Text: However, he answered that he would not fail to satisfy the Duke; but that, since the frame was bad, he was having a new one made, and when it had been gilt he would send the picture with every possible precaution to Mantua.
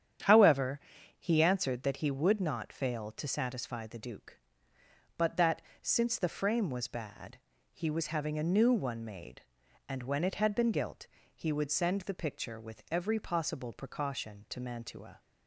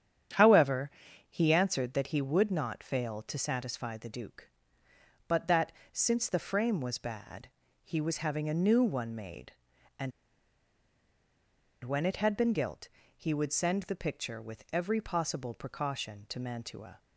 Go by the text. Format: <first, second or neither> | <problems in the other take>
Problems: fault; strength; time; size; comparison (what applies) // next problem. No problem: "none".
first | starts louder than the rest; strong; until 1.7 s; 9 dB; strong in the first // pauses between "and" and "when"; strong; at 10.1 s; 1.7 s long // pauses between "gilt" and "he"; slight; at 12.8 s; 0.28 s long; slight in the first